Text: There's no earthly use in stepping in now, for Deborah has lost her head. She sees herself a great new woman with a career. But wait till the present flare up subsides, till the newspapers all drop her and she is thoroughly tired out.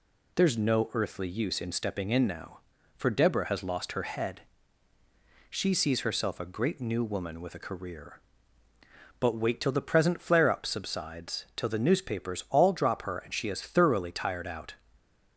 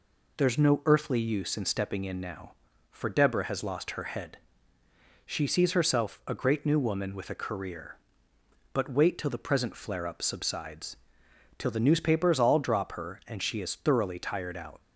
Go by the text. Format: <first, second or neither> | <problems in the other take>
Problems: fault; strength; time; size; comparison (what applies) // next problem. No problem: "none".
neither | none